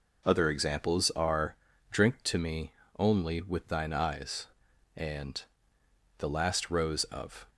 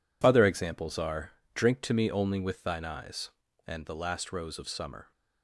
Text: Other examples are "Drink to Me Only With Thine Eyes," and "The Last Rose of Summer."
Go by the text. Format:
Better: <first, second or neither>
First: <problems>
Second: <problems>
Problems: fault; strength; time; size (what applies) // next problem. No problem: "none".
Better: second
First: pauses between "are" and "Drink"; slight; at 1.5 s; 0.34 s long // pauses between "Me" and "Only"; slight; at 2.7 s; 0.26 s long // pauses between "and" and "The"; noticeable; at 5.4 s; 0.76 s long // stops before "Summer"; at 7.4 s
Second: pauses between "are" and "Drink"; slight; at 1.3 s; 0.23 s long